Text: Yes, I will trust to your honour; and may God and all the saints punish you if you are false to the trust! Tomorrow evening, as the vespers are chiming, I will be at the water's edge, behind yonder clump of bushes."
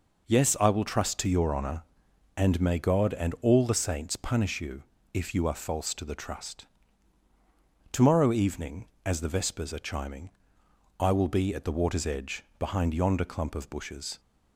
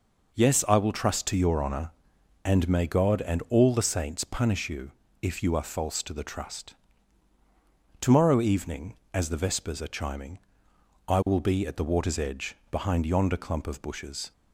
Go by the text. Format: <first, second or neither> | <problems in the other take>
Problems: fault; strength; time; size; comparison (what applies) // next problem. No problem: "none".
neither | pauses between "you" and "if"; slight; the same in both